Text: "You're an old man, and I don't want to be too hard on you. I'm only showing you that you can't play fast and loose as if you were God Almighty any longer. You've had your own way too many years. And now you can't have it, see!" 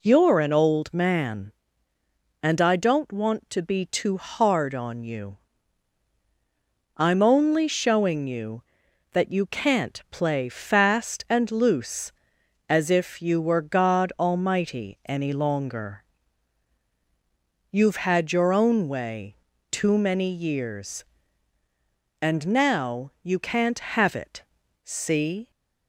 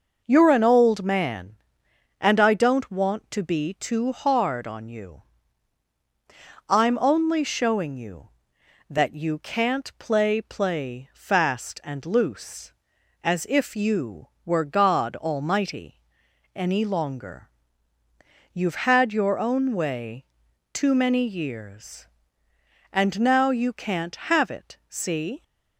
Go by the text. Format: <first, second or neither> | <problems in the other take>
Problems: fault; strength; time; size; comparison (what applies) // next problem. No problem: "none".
first | says "play" twice; at 10.4 s // pauses between "Almighty" and "any"; noticeable; at 15.9 s; 0.56 s long // pauses between "way" and "too"; noticeable; at 20.2 s; 0.48 s long; slight in the first